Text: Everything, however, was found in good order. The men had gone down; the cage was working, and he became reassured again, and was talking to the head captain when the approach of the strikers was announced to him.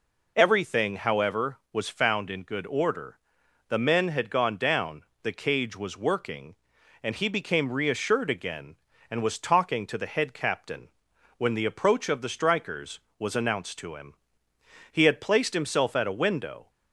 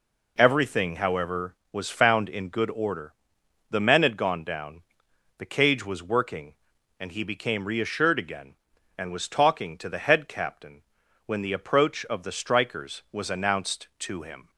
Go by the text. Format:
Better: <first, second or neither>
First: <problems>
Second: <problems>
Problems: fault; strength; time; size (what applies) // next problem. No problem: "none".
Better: second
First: pauses between "captain" and "when"; noticeable; at 10.8 s; 0.48 s long // goes on to say "He had placed himself at a window"; strong; from 14.8 s on; 1.8 s long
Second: pauses between "captain" and "when"; at 10.8 s; 0.42 s long